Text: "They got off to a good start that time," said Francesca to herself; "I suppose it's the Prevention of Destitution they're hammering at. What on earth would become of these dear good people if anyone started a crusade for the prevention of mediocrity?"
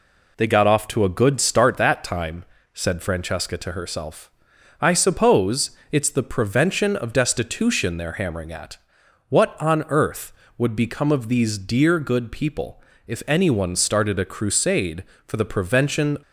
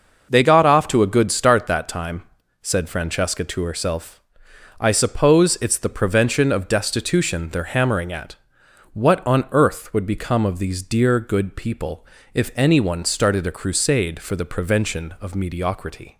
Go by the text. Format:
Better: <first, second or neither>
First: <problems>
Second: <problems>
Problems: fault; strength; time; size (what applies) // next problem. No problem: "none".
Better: second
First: pauses between "people" and "if"; slight; at 12.8 s; 0.24 s long // stops before "of mediocrity"; at 16.2 s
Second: pauses between "people" and "if"; slight; at 12.0 s; 0.28 s long